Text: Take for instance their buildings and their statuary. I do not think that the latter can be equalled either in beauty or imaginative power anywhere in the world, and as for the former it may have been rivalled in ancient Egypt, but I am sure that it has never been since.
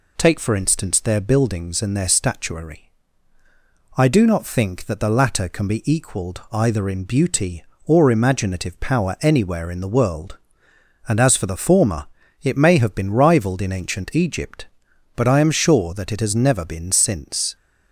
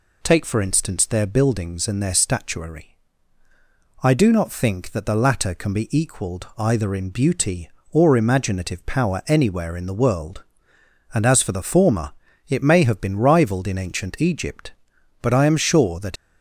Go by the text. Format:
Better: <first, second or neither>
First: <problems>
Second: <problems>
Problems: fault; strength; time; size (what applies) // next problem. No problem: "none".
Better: first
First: pauses between "former" and "it"; slight; at 12.0 s; 0.34 s long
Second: pauses between "former" and "it"; slight; at 12.1 s; 0.34 s long // stops before "it has never been since"; at 16.1 s